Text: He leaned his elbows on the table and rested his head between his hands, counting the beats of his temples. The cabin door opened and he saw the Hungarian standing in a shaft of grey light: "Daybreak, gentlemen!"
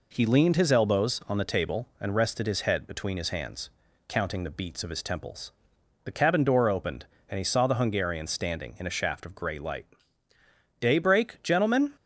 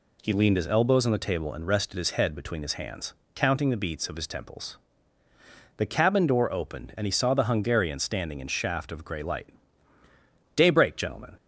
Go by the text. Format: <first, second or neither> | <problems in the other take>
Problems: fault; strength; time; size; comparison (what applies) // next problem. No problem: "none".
first | skips "a"; at 8.4 s